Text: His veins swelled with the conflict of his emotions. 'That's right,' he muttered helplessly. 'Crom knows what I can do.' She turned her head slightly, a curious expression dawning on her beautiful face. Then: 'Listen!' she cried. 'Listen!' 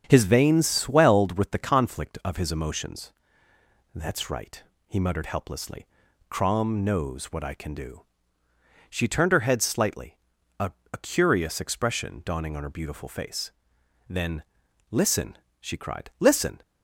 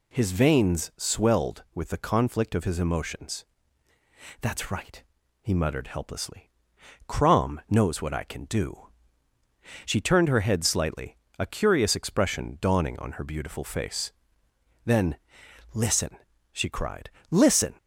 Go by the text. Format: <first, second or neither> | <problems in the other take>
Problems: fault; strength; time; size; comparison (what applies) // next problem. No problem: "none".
second | starts louder than the rest; strong; until 1.0 s; 8 dB // says "a" twice; at 10.9 s